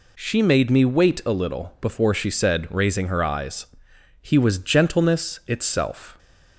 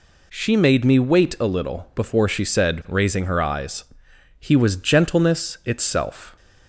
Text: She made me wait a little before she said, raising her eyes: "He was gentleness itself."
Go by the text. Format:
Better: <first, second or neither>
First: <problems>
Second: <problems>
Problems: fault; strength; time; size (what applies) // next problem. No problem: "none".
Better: neither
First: none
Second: none